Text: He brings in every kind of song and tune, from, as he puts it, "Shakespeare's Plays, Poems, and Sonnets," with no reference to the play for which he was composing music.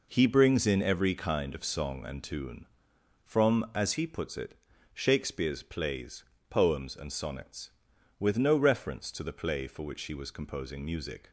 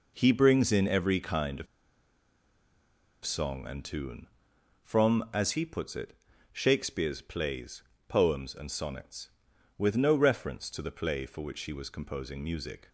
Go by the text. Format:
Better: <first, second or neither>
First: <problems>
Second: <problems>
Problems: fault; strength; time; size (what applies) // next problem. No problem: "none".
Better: first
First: none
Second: pauses between "of" and "song"; strong; at 1.6 s; 1.5 s long